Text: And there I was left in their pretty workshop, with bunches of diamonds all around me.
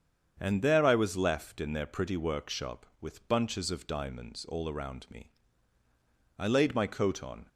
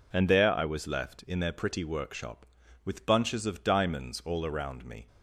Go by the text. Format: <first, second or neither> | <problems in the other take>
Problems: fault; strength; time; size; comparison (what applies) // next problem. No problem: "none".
second | starts louder than the rest; strong; until 1.4 s; 7.5 dB // goes on to say "I laid my coat on"; noticeable; from 6.3 s on; 1.1 s long